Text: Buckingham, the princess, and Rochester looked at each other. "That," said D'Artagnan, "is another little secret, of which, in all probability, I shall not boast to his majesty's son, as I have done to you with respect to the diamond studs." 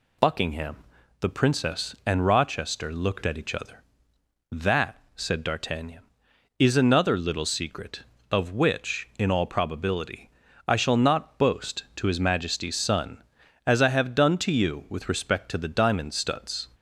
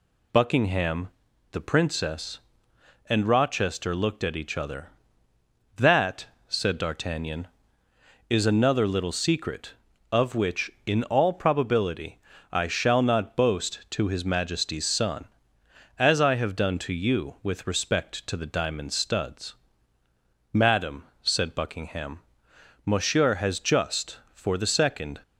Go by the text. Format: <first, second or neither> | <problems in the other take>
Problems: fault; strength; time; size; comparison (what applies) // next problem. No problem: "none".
first | goes on to say "Madam said Buckingham monsieur has just for the second"; strong; from 20.5 s on; 4.6 s long